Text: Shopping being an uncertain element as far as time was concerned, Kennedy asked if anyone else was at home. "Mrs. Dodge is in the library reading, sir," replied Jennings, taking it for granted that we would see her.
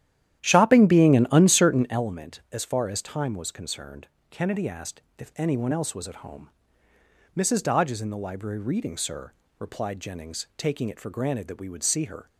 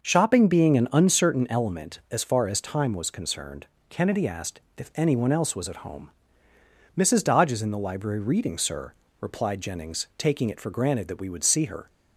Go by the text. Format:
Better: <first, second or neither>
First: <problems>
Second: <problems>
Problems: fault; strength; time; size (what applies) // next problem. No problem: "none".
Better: second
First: starts louder than the rest; strong; until 2.1 s; 11.5 dB // pauses between "asked" and "if"; slight; at 5.0 s; 0.16 s long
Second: pauses between "asked" and "if"; slight; at 4.6 s; 0.16 s long